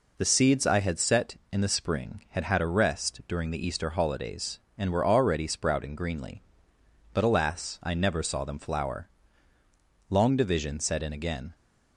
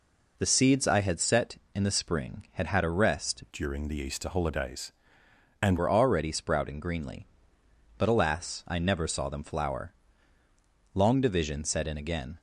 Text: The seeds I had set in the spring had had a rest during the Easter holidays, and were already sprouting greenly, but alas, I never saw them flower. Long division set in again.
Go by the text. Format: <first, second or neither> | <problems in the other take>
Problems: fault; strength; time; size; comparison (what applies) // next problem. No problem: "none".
first | changes voice from "during" to "and"; from 3.5 to 5.7 s; 2.2 s long